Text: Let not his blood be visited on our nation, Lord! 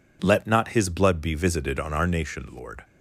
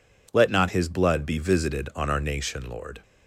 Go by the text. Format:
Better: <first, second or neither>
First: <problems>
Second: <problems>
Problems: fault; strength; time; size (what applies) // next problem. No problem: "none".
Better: neither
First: none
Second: none